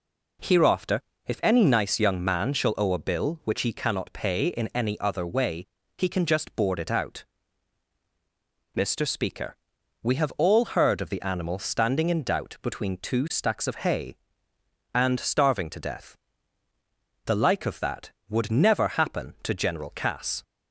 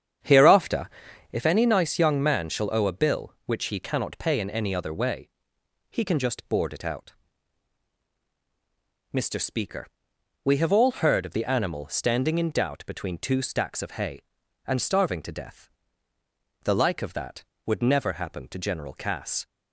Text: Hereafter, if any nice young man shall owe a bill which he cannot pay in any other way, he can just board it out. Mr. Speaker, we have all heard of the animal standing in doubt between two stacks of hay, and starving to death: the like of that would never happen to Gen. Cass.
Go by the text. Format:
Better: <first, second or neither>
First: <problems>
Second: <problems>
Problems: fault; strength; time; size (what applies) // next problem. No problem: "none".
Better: first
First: none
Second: starts louder than the rest; strong; until 1.4 s; 8.5 dB